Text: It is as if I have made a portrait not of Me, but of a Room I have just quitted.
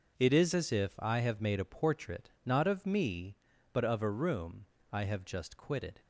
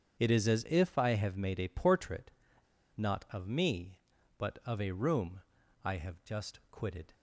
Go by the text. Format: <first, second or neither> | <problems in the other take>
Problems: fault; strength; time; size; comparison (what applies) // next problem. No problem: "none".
first | starts louder than the rest; strong; until 1.2 s; 7 dB // pauses between "portrait" and "not"; noticeable; at 2.2 s; 0.67 s long // pauses between "Room" and "I"; at 5.4 s; 0.42 s long; slight in the first